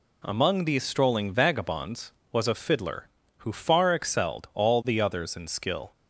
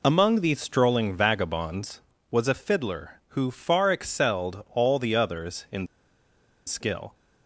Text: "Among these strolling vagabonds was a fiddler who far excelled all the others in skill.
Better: first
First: none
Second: pauses between "in" and "skill"; noticeable; at 5.8 s; 0.80 s long

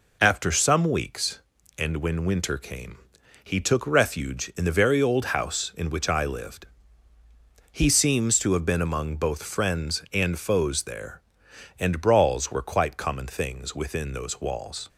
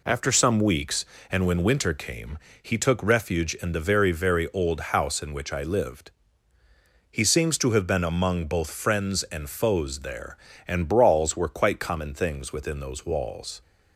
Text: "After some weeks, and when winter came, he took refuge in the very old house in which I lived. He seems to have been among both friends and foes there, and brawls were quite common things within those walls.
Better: first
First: none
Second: says "very" twice; at 4.1 s

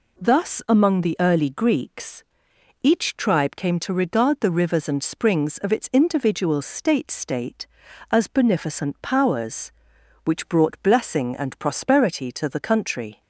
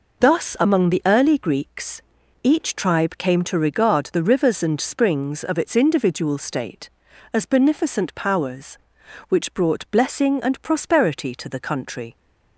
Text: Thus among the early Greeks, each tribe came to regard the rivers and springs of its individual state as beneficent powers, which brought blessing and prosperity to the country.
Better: second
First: says "state" twice; at 7.1 s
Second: none

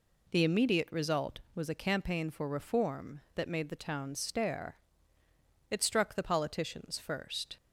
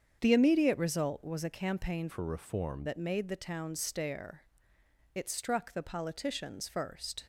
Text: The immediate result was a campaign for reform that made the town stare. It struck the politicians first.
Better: first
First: none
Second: starts louder than the rest; strong; until 1.2 s; 7.5 dB // changes voice from "for" to "reform"; from 2.0 to 2.8 s; 0.8 s long

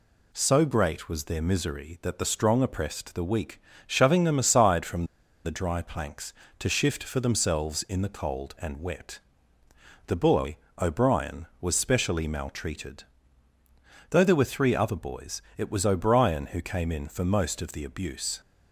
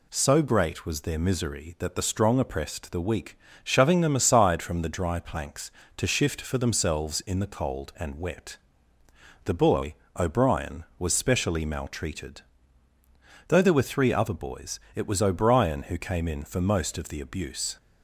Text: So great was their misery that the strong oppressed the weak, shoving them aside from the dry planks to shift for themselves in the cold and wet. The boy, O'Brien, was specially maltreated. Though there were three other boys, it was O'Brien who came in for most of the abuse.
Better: second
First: pauses between "from" and "the"; at 5.0 s; 0.40 s long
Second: none

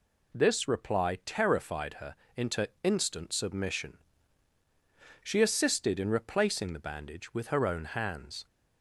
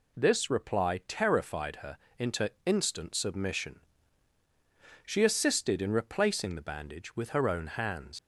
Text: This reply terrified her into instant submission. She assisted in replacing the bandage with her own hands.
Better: first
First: pauses between "her" and "into"; slight; at 2.1 s; 0.20 s long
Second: pauses between "her" and "into"; slight; at 1.9 s; 0.20 s long // leaves "hands" unfinished; at 8.1 s; 90 ms

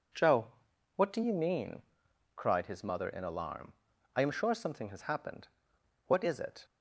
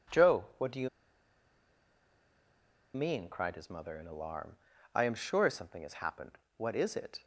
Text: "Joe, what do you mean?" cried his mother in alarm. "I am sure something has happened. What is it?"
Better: first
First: none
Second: pauses between "you" and "mean"; strong; at 0.8 s; 2.0 s long

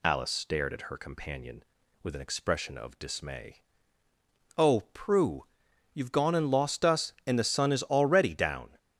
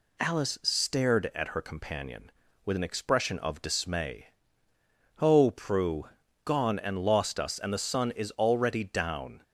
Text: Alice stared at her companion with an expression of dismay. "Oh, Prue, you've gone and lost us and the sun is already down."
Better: first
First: none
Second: skips "you've"; at 6.2 s

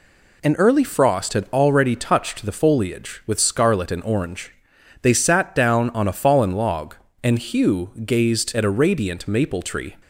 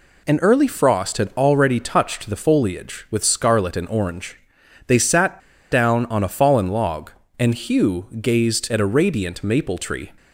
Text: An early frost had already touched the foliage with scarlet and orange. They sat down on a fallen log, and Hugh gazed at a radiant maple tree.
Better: first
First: none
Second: pauses between "sat" and "down"; slight; at 5.3 s; 0.33 s long

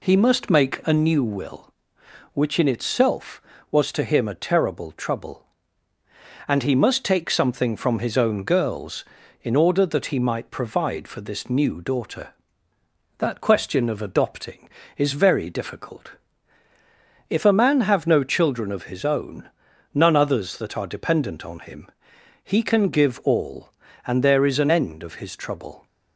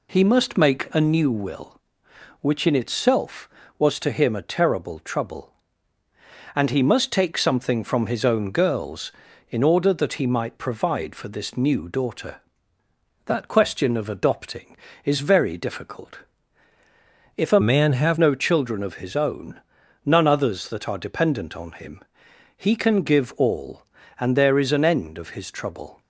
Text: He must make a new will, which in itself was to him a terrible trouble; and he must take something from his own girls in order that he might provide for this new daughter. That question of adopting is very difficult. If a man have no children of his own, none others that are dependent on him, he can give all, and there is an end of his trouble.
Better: first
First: none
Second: changes voice from "man" to "have"; from 17.6 to 18.1 s; 0.5 s long

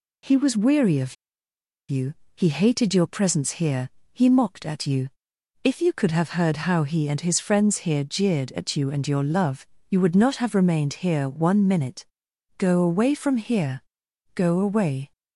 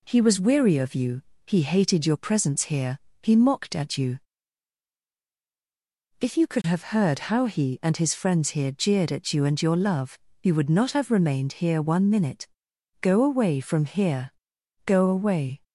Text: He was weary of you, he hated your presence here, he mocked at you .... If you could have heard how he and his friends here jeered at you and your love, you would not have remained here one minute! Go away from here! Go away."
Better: second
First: pauses between "of" and "you"; noticeable; at 1.1 s; 0.76 s long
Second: none

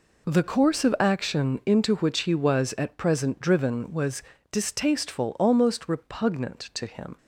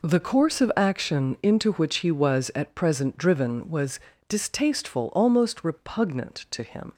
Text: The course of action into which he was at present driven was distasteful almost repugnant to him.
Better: neither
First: pauses between "was" and "distasteful"; slight; at 4.2 s; 0.30 s long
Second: pauses between "was" and "distasteful"; slight; at 3.9 s; 0.30 s long

